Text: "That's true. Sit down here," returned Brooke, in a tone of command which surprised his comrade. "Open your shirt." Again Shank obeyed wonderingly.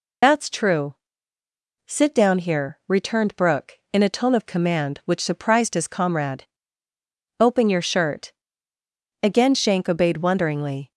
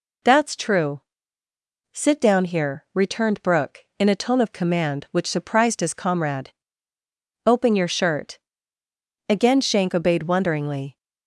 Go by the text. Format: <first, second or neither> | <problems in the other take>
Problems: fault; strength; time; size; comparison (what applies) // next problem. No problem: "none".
second | loses the start of "That's"; at 0.2 s; 45 ms